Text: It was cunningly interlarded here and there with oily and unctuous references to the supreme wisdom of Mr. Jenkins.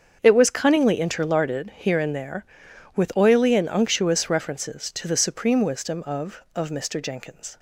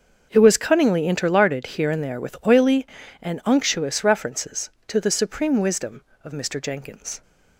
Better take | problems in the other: second | starts louder than the rest; until 1.2 s; 7 dB; also in the second // says "of" twice; at 6.5 s

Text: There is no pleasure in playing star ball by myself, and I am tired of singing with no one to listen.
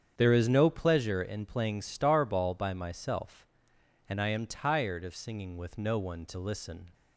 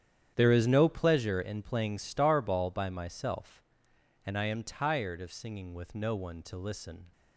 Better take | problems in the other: first | gets quieter; strong; throughout; 15 dB // starts louder than the rest; strong; until 1.3 s; 10 dB; strong in the first

